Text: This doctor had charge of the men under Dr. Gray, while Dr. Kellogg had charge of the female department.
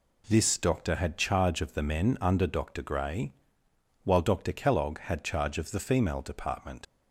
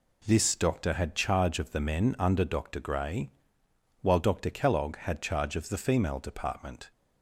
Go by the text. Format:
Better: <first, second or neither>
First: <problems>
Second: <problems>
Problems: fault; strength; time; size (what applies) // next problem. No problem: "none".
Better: second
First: leaves "department" unfinished; at 6.8 s; 80 ms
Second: none